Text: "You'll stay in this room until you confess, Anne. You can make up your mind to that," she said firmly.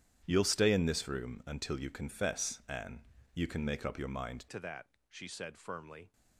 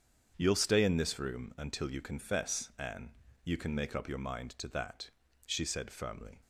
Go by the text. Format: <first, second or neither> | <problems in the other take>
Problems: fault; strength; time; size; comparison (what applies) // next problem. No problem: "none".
second | starts louder than the rest; strong; until 1.2 s; 10 dB; strong in the second // changes voice at "to"; from 4.5 s on; 1.6 s long